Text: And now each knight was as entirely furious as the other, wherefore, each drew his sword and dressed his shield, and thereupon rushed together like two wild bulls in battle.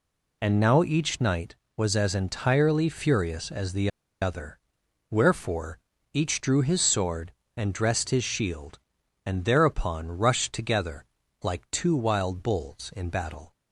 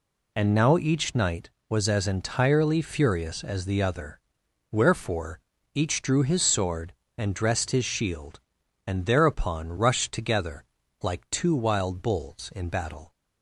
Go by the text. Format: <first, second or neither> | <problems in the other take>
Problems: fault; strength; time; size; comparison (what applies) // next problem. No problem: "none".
second | pauses between "the" and "other"; slight; at 3.8 s; 0.32 s long // pauses between "together" and "like"; at 11.0 s; 0.38 s long; also in the second